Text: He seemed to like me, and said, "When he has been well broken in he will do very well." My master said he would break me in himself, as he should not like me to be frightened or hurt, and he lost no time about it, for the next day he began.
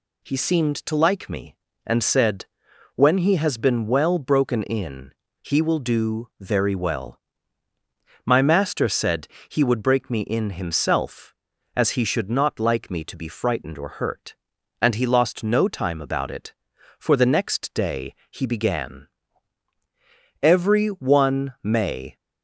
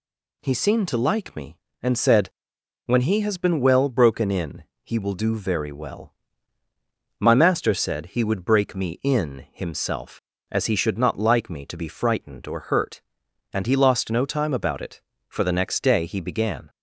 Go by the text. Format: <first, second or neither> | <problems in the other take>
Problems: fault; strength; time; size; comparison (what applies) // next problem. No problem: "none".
second | pauses between "in" and "he"; slight; at 5.1 s; 0.30 s long; slight in the second // pauses between "said" and "he"; slight; at 9.2 s; 0.22 s long // pauses between "day" and "he"; slight; at 18.1 s; 0.16 s long // goes on to say "Every one may"; strong; from 20.4 s on; 1.7 s long